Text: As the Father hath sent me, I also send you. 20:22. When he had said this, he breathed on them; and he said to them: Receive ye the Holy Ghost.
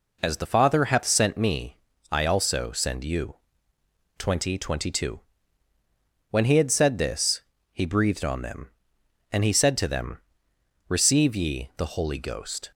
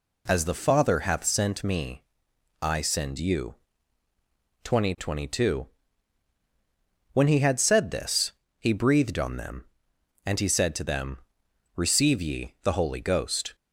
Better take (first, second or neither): first